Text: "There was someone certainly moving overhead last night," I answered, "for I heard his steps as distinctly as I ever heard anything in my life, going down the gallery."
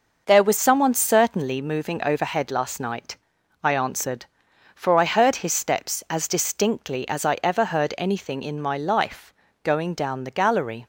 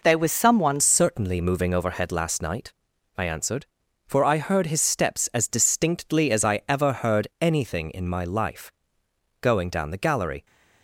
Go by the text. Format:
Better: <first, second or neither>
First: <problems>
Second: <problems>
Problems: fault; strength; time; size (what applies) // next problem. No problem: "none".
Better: first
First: none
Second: changes voice at "certainly"; from 0.7 s on; 9.7 s long